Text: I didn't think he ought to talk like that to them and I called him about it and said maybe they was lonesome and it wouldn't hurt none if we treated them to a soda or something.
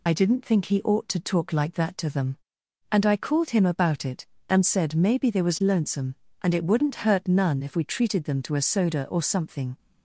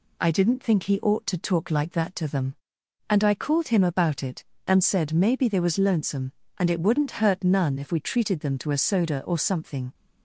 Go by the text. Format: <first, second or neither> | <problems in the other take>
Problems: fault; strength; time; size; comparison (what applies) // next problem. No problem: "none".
second | loses the start of "I"; at 0.0 s; 30 ms